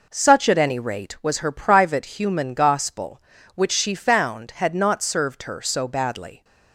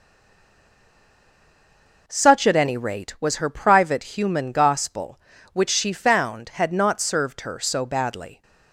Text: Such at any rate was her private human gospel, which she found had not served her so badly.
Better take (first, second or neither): first